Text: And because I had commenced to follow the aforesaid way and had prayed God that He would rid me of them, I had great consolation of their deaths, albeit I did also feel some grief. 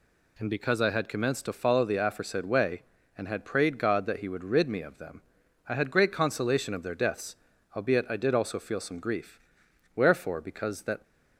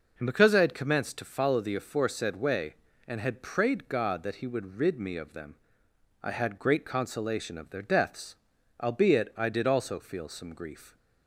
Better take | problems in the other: second | goes on to say "Wherefore because that"; noticeable; from 9.9 s on; 1.0 s long

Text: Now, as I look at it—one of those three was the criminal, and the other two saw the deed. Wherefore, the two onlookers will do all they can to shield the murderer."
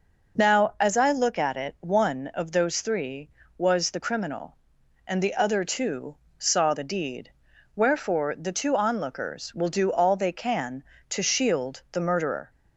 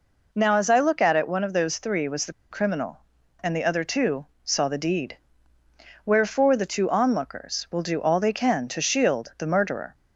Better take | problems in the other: first | pauses between "the" and "criminal"; slight; at 2.3 s; 0.19 s long // pauses between "two" and "saw"; slight; at 4.2 s; 0.18 s long; slight in the first

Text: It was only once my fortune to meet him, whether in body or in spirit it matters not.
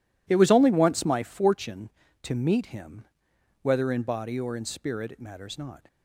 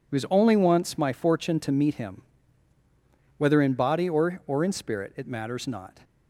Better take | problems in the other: first | says "or" twice; at 4.4 s

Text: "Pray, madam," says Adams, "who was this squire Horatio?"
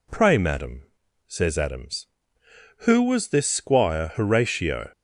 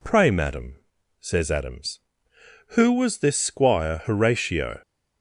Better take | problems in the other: neither | none

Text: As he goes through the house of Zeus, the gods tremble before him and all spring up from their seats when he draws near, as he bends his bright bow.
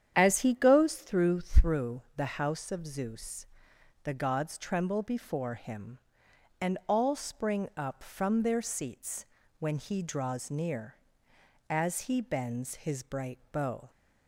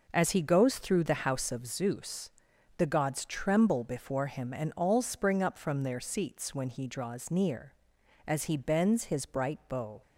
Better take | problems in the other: second | starts louder than the rest; strong; until 1.1 s; 9 dB // says "through" twice; at 1.4 s // pauses between "seats" and "when"; slight; at 9.2 s; 0.32 s long

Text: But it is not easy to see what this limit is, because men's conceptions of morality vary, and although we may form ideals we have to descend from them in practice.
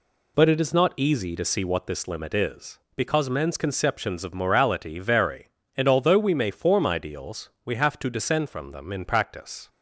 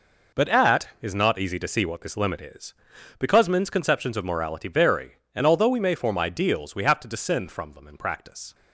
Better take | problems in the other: first | says "at" for "it"; at 0.4 s

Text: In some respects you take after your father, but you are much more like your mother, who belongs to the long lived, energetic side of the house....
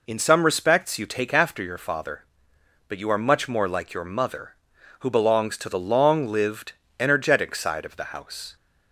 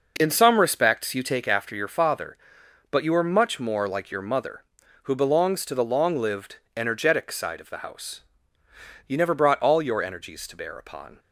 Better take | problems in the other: first | goes on to say "You never brought all your energies to bear upon"; strong; from 9.0 s on; 2.1 s long

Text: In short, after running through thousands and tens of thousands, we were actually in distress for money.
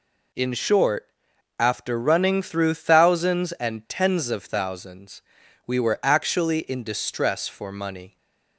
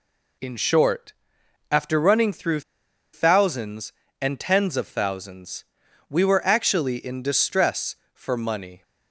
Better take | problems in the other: first | pauses between "through" and "thousands"; noticeable; at 2.6 s; 0.52 s long

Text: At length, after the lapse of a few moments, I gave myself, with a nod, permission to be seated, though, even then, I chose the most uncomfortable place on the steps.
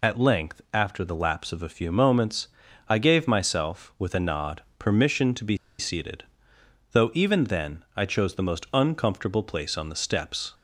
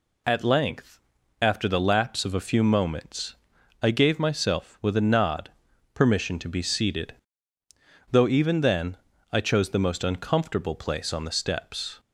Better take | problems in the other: second | pauses between "be" and "seated"; slight; at 5.5 s; 0.22 s long

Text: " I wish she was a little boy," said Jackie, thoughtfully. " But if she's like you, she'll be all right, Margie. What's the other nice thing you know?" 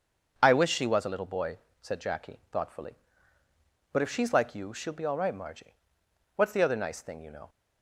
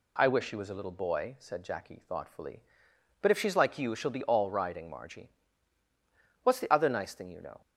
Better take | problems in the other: first | says "riding" for "right"; at 4.4 s

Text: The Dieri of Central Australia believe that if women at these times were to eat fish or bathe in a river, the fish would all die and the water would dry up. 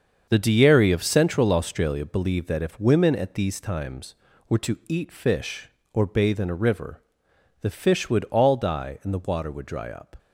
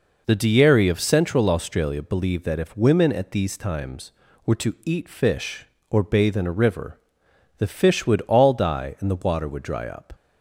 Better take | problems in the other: second | gets quieter; strong; throughout; 9.5 dB

